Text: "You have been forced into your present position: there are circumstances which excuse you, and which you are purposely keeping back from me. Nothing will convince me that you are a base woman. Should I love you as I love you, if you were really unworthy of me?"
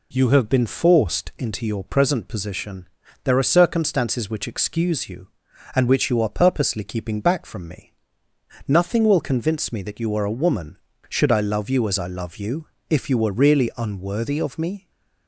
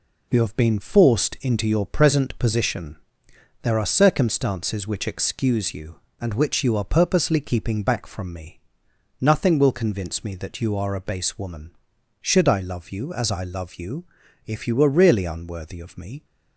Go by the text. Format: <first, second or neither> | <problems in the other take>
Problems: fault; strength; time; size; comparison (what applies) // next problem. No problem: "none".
second | skips "base"; at 10.3 s